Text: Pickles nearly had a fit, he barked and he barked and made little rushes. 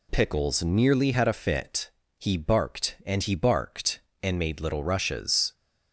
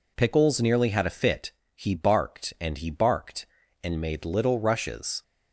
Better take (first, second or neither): neither